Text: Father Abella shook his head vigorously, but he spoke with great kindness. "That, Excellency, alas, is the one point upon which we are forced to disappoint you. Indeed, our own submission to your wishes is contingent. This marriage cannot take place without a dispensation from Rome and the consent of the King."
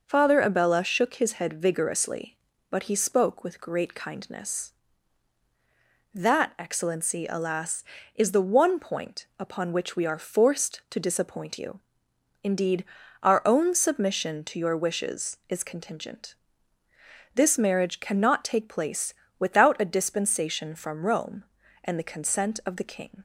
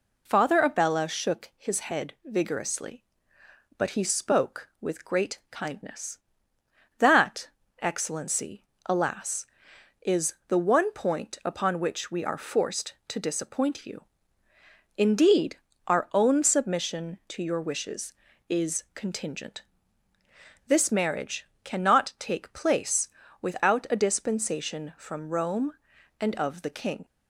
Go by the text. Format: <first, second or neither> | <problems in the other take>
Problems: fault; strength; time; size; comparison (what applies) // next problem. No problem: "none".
first | pauses between "marriage" and "cannot"; slight; at 21.4 s; 0.20 s long // pauses between "place" and "without"; slight; at 23.0 s; 0.34 s long; slight in the first // skips "the consent"; at 26.3 s